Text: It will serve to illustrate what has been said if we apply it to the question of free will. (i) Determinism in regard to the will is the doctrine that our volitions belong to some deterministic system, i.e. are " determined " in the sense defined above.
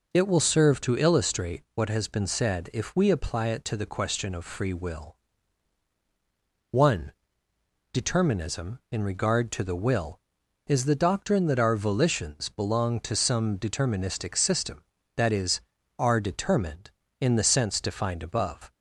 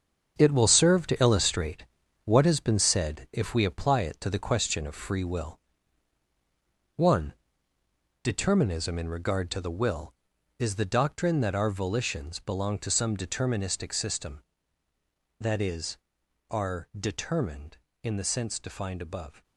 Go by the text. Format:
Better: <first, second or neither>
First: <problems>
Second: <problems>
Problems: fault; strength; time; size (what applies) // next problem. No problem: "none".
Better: first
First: none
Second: gets quieter; strong; throughout; 11 dB // pauses between "illustrate" and "what"; at 1.8 s; 0.40 s long